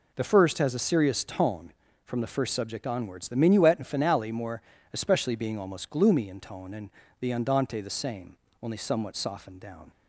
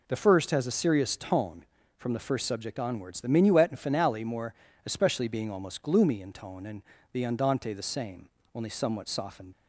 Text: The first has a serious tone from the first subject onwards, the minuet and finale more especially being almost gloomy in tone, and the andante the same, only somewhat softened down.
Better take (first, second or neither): first